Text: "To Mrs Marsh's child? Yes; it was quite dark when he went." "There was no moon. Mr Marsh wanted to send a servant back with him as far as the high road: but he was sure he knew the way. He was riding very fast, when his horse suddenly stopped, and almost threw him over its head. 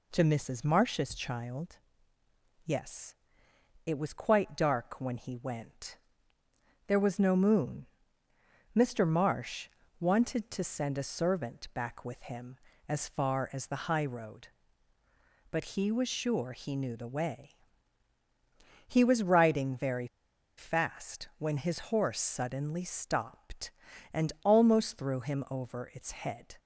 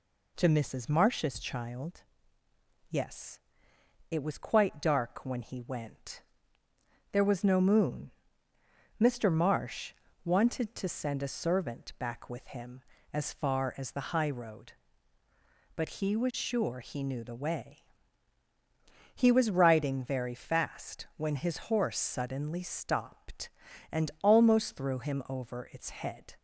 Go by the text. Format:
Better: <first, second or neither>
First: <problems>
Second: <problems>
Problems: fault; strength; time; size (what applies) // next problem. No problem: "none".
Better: second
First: pauses between "Marsh" and "wanted"; slight; at 9.6 s; 0.32 s long // pauses between "very" and "fast"; noticeable; at 20.0 s; 0.49 s long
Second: pauses between "Marsh" and "wanted"; slight; at 9.9 s; 0.32 s long